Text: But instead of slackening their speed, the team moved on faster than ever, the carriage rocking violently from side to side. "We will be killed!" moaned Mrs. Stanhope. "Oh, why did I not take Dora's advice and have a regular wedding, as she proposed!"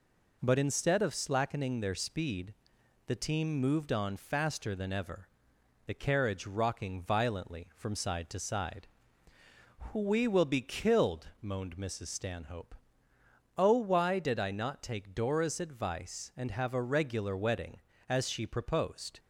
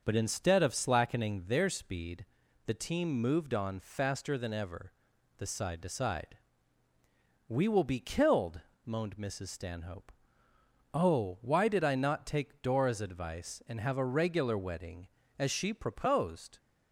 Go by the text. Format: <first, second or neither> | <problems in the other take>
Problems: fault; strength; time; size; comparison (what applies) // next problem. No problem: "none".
first | skips "carriage rocking violently from"; at 5.4 s